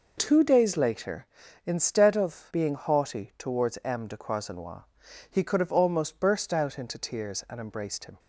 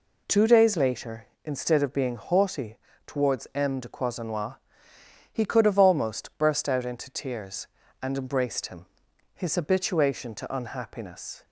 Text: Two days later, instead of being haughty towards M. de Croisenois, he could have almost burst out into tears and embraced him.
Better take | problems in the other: first | pauses between "haughty" and "towards"; slight; at 2.7 s; 0.30 s long // goes on to say "His habituation to unhappiness"; strong; from 9.3 s on; 2.1 s long

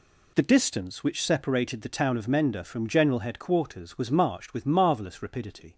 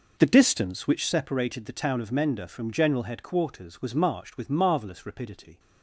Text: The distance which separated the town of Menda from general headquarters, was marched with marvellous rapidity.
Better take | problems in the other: first | starts louder than the rest; noticeable; until 1.1 s; 5.5 dB

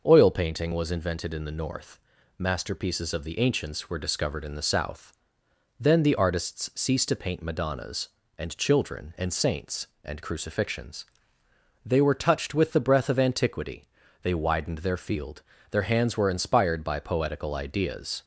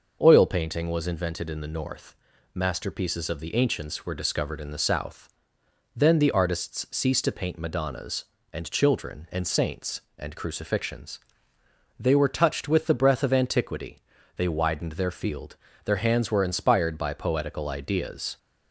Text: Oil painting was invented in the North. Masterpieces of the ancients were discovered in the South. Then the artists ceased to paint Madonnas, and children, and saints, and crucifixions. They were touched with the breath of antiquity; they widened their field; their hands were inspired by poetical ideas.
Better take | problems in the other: neither | none

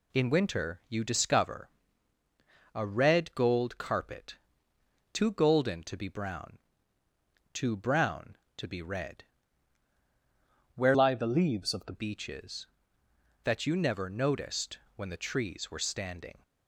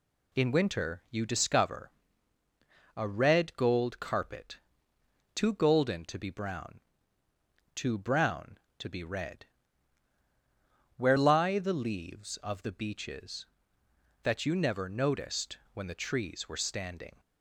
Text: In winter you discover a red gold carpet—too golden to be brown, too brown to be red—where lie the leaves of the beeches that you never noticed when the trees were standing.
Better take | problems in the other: second | pauses between "discover" and "a"; at 1.6 s; 1.0 s long; also in the second // changes voice from "lie" to "the"; from 10.9 to 11.9 s; 1.0 s long // pauses between "noticed" and "when"; slight; at 14.7 s; 0.18 s long; slight in the second

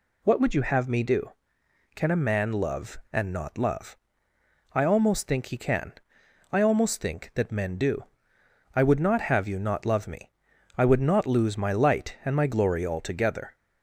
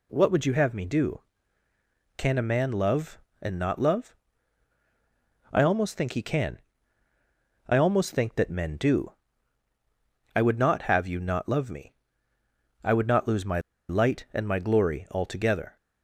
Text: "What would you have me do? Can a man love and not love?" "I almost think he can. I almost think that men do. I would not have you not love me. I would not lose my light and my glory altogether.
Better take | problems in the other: first | pauses between "my" and "light"; slight; at 13.6 s; 0.28 s long

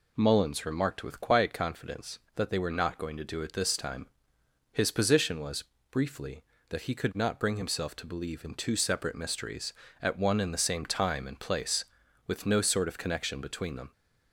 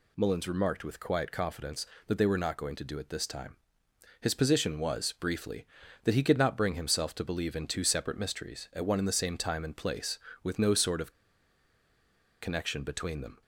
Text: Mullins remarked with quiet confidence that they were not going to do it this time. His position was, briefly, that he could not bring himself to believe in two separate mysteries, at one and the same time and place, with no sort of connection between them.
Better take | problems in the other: first | pauses between "of" and "connection"; strong; at 11.1 s; 1.2 s long

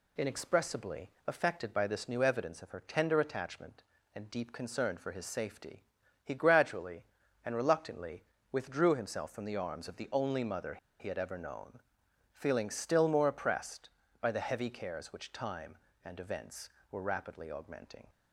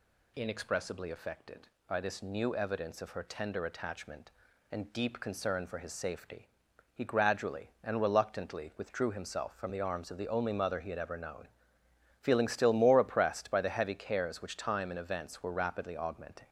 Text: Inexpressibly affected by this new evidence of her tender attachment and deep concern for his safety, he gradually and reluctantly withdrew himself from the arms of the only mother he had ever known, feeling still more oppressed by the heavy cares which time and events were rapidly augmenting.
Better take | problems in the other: second | pauses between "Inexpressibly" and "affected"; slight; at 1.0 s; 0.18 s long // pauses between "reluctantly" and "withdrew"; slight; at 8.2 s; 0.26 s long // pauses between "mother" and "he"; slight; at 10.7 s; 0.21 s long

